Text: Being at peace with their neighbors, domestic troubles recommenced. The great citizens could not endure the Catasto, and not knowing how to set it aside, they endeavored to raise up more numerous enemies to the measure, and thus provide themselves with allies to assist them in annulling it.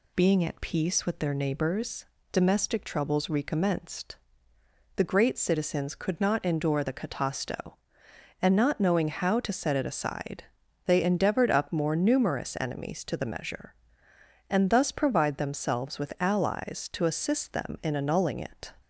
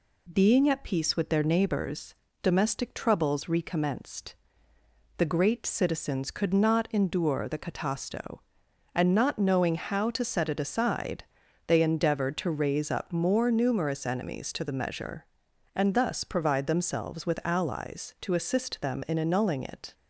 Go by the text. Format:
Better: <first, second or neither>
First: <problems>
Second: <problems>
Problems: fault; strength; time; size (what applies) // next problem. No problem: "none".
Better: second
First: skips "to raise"; at 11.5 s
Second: none